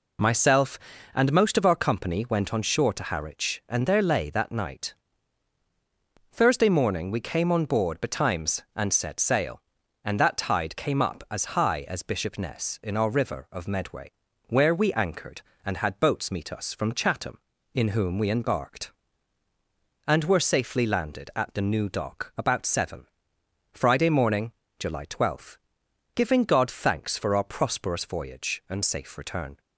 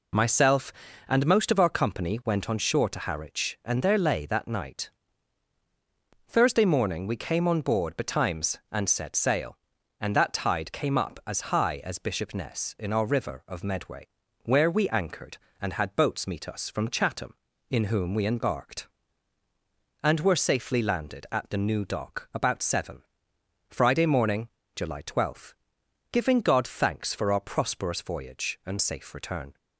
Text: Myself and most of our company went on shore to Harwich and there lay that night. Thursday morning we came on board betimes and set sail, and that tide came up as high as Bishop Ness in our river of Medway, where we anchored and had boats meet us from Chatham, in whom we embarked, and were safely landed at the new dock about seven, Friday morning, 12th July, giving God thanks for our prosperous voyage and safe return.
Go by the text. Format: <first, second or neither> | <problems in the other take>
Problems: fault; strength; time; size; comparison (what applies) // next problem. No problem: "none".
neither | none